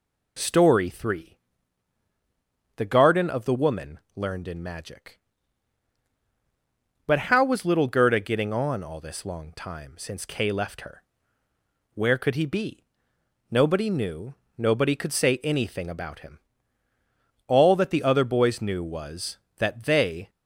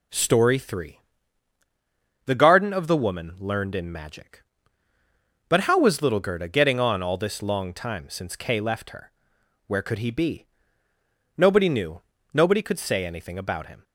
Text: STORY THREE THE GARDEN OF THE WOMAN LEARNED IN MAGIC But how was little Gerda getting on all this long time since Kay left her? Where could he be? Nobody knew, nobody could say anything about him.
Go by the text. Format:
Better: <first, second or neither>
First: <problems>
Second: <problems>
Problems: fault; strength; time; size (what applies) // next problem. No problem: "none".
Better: second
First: pauses between "THREE" and "THE"; strong; at 1.3 s; 1.4 s long // pauses between "WOMAN" and "LEARNED"; slight; at 3.9 s; 0.18 s long // goes on to say "All that the other boys knew was that they"; strong; from 17.4 s on; 2.8 s long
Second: pauses between "THREE" and "THE"; strong; at 0.9 s; 1.2 s long